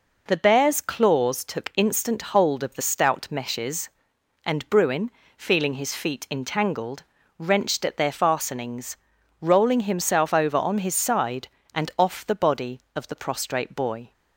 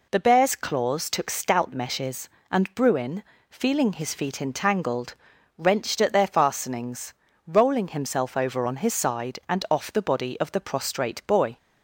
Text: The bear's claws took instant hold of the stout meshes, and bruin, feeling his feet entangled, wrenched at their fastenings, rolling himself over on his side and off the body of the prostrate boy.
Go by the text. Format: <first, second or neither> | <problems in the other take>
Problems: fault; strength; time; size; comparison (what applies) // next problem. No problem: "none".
first | skips "instant hold of the"; at 1.2 s